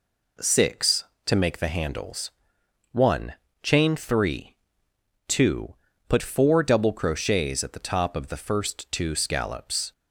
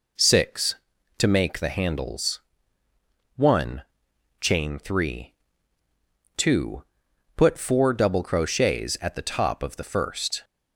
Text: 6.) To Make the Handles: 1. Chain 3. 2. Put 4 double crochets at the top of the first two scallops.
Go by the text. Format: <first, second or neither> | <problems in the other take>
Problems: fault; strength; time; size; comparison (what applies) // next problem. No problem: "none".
first | stops before "two scallops"; at 10.4 s